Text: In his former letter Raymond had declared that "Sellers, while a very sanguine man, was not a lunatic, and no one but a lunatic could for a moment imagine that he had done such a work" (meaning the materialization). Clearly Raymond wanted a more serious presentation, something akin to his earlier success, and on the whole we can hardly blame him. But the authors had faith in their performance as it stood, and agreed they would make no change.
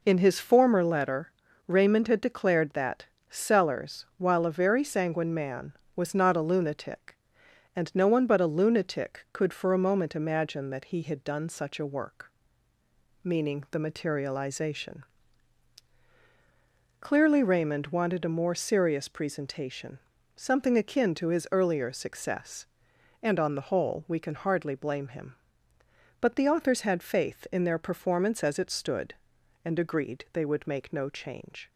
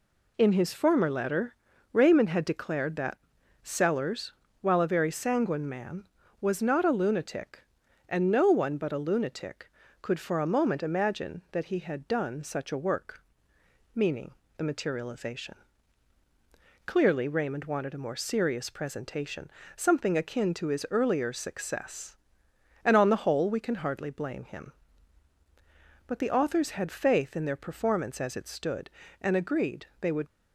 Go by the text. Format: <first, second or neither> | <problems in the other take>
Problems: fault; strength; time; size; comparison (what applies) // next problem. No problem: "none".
first | pauses between "letter" and "Raymond"; at 1.5 s; 0.38 s long; also in the first // pauses between "that" and "Sellers"; at 3.1 s; 0.44 s long; slight in the first // pauses between "meaning" and "the"; slight; at 14.3 s; 0.22 s long // pauses between "agreed" and "they"; slight; at 29.8 s; 0.16 s long // stops before "make no change"; at 30.2 s